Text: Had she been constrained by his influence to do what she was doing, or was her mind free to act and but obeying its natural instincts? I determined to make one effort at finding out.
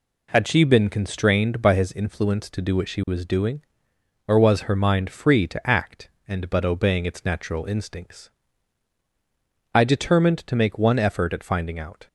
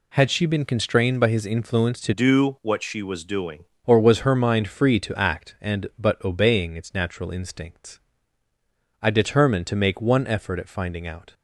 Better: first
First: none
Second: changes voice from "do" to "doing"; from 2.1 to 3.6 s; 1.5 s long

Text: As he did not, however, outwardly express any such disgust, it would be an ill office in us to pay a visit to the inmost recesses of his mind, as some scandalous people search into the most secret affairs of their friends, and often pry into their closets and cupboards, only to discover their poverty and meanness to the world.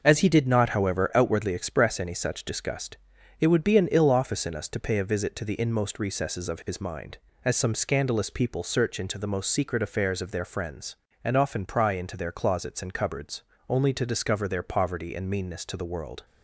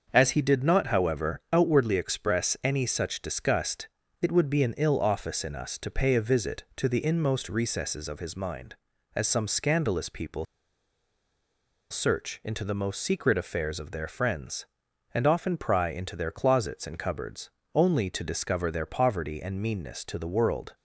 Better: first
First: none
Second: starts louder than the rest; until 1.1 s; 6.5 dB // pauses between "people" and "search"; strong; at 10.4 s; 1.4 s long

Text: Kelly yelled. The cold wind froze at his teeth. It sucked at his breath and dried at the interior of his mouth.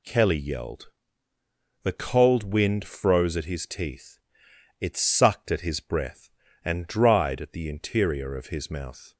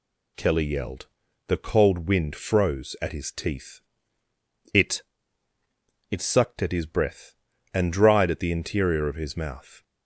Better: first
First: none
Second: says "It" twice; at 6.0 s

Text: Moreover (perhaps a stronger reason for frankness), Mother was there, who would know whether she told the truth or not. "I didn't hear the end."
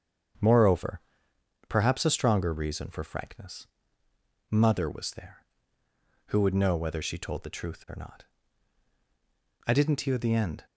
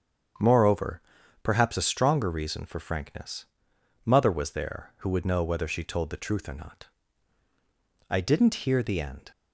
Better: neither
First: starts louder than the rest; strong; until 2.0 s; 7.5 dB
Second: starts louder than the rest; strong; until 1.8 s; 7.5 dB

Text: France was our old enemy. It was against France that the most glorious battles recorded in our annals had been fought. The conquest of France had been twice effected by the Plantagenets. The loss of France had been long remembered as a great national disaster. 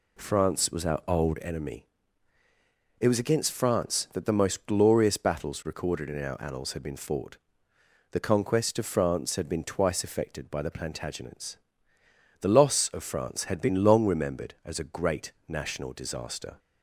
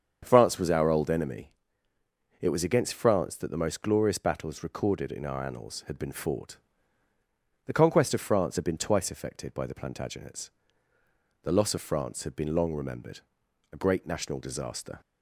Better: first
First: none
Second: starts louder than the rest; strong; until 1.2 s; 7.5 dB // skips "as"; at 13.4 s

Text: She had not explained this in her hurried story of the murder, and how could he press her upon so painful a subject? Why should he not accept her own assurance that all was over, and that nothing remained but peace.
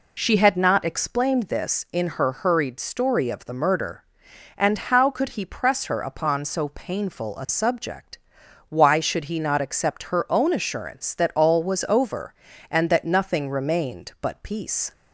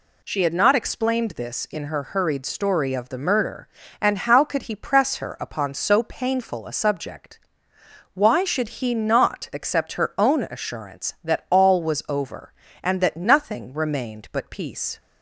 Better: neither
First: none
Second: none

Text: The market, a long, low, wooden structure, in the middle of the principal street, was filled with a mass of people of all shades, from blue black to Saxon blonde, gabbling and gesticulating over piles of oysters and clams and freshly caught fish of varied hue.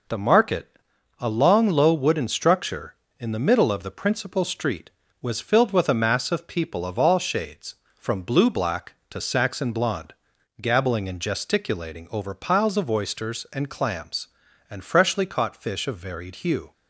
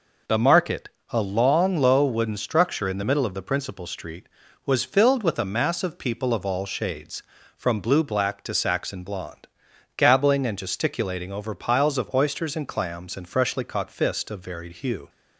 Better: first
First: none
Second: says "fist" for "fish"; at 13.9 s

